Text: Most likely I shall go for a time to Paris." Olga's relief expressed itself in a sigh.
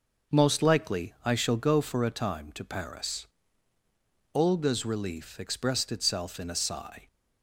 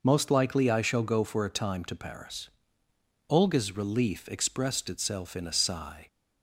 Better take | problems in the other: neither | none

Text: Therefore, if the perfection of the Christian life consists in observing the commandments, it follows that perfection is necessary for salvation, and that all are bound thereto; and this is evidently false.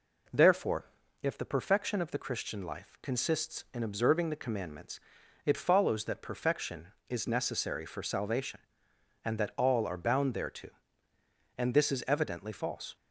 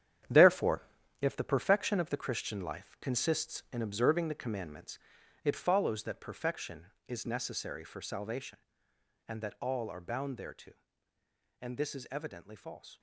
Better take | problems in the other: first | gets quieter; strong; throughout; 9 dB

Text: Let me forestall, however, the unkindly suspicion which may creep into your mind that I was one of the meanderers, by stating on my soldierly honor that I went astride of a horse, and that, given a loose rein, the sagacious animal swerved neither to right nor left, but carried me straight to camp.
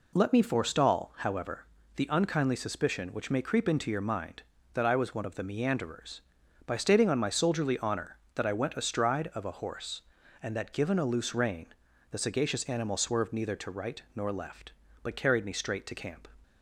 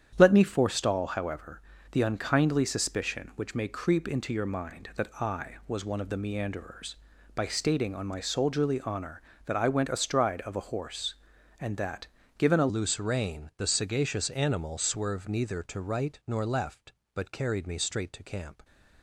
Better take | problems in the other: first | starts louder than the rest; strong; until 1.1 s; 9 dB // changes voice at "loose"; from 12.6 s on; 6.0 s long

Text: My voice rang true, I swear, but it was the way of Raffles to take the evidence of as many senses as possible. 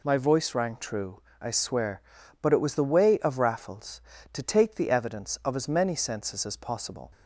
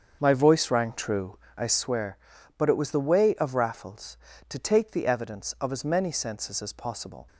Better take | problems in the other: first | starts louder than the rest; until 1.8 s; 7 dB

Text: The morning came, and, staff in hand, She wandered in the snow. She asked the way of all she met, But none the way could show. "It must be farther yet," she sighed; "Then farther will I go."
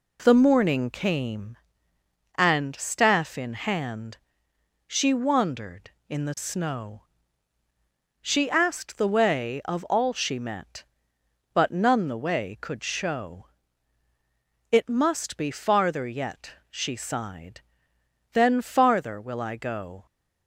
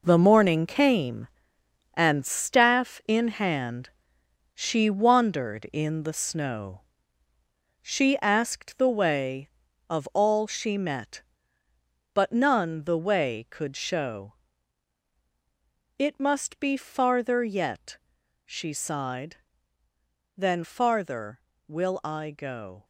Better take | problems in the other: first | gets quieter; strong; throughout; 9.5 dB

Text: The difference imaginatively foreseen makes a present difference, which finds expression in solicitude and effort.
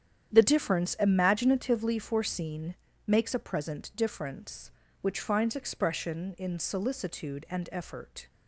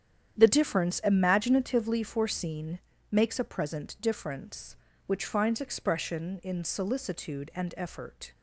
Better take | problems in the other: neither | starts louder than the rest; strong; the same in both // pauses between "foreseen" and "makes"; slight; the same in both

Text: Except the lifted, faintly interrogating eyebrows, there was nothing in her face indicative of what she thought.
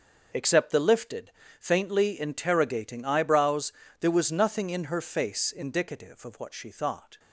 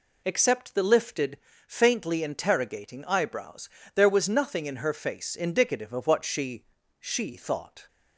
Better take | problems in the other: first | says "she" twice; at 6.9 s

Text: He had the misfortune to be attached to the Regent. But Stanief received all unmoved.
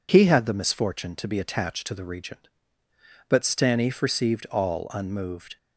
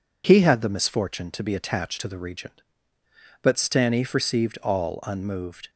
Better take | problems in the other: neither | none

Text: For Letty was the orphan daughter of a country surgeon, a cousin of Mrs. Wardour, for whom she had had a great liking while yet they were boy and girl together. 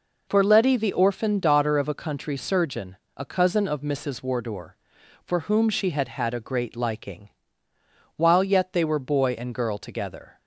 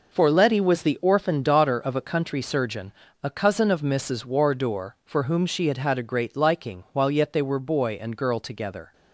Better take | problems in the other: second | skips "was"; at 0.7 s // pauses between "liking" and "while"; noticeable; at 7.2 s; 0.88 s long

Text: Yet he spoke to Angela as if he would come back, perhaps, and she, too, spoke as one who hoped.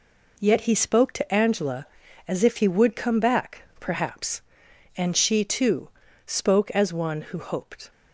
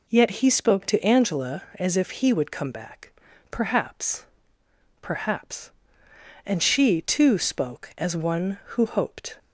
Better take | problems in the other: first | says "perhaps" twice; at 5.0 s

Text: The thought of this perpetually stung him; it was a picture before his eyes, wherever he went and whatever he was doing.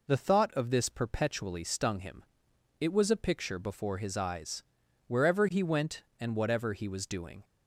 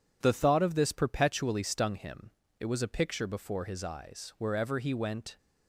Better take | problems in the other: first | stops before "and whatever he was doing"; at 5.3 s

